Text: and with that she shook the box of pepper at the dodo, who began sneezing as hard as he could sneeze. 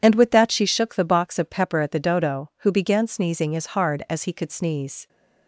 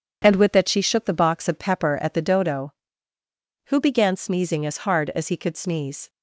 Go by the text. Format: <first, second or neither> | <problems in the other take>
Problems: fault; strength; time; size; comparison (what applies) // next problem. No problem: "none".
neither | none